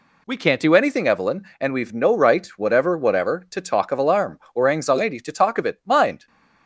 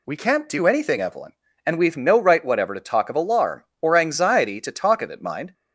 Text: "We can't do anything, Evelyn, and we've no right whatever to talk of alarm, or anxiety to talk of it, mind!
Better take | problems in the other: second | says "whatever" twice; at 2.9 s

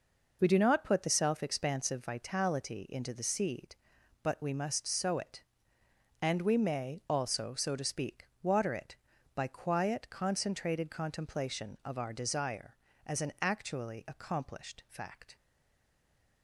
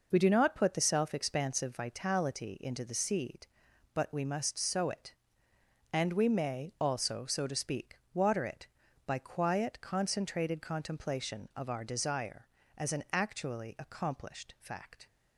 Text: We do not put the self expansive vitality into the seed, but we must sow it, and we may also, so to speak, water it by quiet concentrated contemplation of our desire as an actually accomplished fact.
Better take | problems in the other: second | stays silent after the last word; from 15.3 s on; 1.1 s long

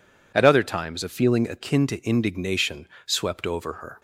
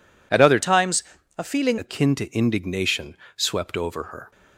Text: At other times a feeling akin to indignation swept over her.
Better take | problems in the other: first | changes voice from "times" to "feeling"; from 0.5 to 1.7 s; 1.2 s long // pauses between "times" and "a"; slight; at 1.0 s; 0.34 s long // pauses between "indignation" and "swept"; slight; at 3.1 s; 0.22 s long; slight in the first

